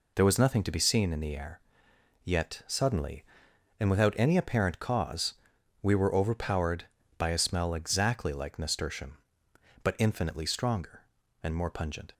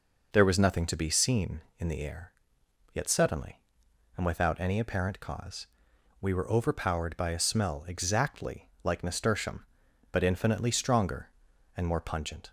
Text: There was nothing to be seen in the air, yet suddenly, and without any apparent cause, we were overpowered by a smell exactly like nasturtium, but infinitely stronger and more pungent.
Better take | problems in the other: neither | none

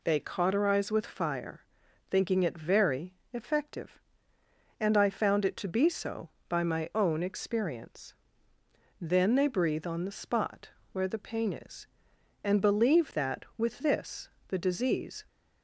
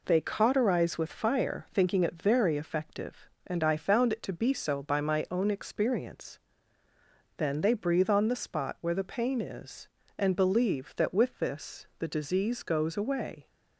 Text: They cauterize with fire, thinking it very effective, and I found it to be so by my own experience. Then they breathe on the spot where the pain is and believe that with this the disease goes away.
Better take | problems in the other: second | pauses between "very" and "effective"; slight; at 3.1 s; 0.20 s long // pauses between "spot" and "where"; slight; at 10.6 s; 0.22 s long // pauses between "this" and "the"; slight; at 14.2 s; 0.18 s long // stops before "goes away"; at 15.2 s

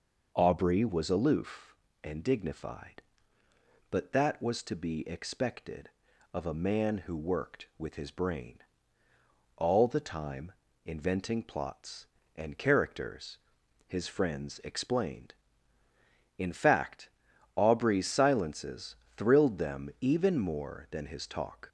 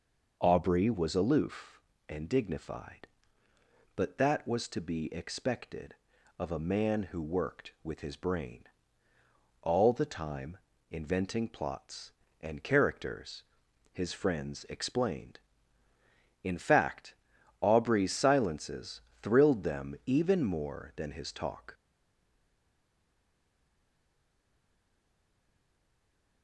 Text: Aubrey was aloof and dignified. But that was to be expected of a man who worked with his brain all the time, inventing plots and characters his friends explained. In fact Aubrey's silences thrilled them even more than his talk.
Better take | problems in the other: first | pauses between "brain" and "all"; at 8.6 s; 1.0 s long; also in the first // pauses between "characters" and "his"; noticeable; at 13.4 s; 0.50 s long; noticeable in the first // pauses between "fact" and "Aubrey's"; at 17.1 s; 0.44 s long; also in the first // pauses between "silences" and "thrilled"; slight; at 18.9 s; 0.24 s long; slight in the first // stays silent after the last word; strong; from 21.7 s on; 4.7 s long

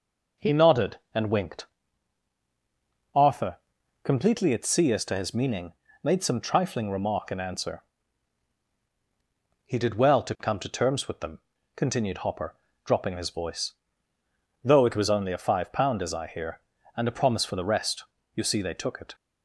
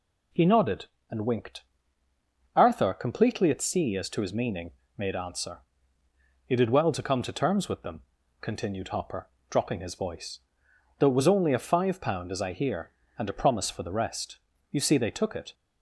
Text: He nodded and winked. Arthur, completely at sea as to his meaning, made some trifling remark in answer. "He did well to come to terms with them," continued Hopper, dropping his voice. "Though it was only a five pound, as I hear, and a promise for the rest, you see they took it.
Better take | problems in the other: first | skips "some trifling remark in"; at 5.1 s

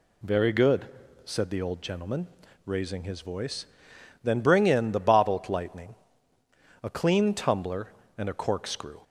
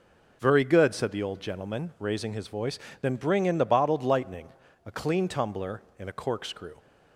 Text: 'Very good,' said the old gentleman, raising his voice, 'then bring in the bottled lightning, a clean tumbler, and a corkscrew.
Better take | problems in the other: neither | none

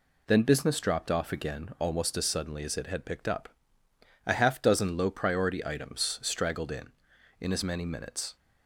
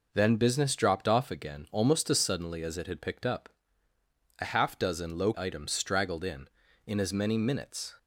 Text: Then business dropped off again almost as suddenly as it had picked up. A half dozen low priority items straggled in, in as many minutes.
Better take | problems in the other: first | skips "priority"; at 5.3 s

